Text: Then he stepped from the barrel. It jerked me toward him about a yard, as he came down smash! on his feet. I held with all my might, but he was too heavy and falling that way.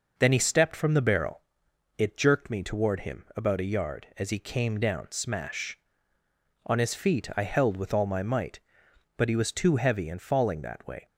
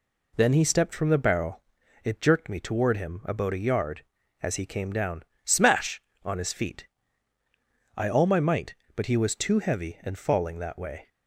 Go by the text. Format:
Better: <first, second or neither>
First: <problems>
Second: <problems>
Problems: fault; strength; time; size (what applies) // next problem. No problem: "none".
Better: first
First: none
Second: pauses between "down" and "smash"; slight; at 5.2 s; 0.22 s long // skips "held with"; at 8.0 s